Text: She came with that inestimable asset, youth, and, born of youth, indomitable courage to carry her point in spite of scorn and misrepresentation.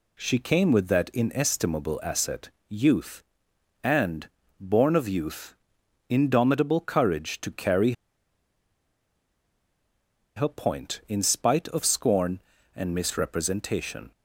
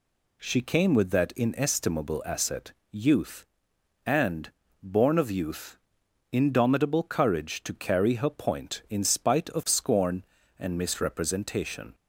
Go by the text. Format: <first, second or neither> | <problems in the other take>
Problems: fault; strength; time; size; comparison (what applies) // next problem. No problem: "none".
second | pauses between "carry" and "her"; strong; at 7.9 s; 2.4 s long